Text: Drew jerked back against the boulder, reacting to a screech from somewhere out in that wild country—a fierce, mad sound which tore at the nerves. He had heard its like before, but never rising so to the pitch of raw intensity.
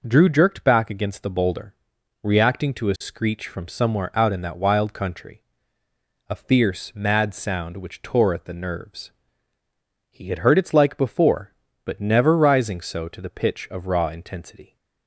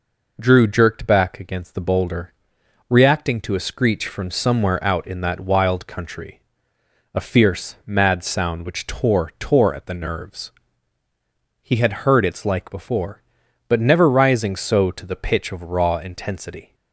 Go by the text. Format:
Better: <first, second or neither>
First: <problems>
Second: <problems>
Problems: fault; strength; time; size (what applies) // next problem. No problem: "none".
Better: first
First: none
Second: says "tore" twice; at 9.3 s